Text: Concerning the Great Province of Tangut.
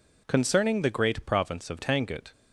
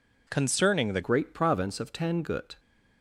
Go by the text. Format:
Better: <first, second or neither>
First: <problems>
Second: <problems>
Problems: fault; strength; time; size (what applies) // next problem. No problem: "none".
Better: first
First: none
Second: changes voice at "Great"; from 1.0 s on; 1.5 s long